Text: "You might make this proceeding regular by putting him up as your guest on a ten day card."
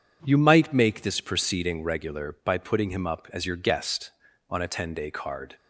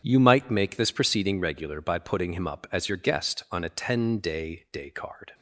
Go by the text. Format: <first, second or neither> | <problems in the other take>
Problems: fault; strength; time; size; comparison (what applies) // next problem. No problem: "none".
first | starts louder than the rest; strong; until 1.0 s; 8.5 dB // says "day" twice; at 4.6 s